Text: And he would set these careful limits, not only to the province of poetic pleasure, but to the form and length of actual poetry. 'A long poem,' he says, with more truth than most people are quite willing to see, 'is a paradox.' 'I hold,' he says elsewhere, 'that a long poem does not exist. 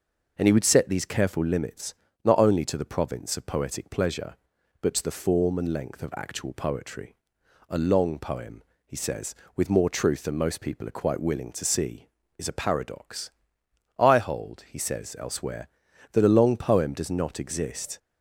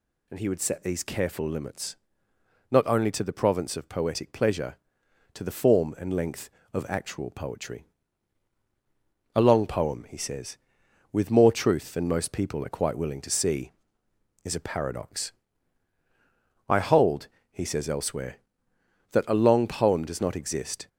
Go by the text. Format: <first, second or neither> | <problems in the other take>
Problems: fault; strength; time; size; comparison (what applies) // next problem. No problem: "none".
first | skips "but"; at 5.0 s